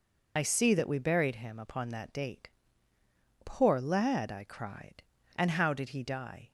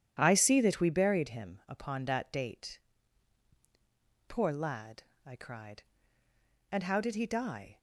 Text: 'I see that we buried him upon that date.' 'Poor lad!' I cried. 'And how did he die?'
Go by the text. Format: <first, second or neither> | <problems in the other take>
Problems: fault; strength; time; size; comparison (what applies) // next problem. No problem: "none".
second | loses the start of "I"; at 0.3 s; 50 ms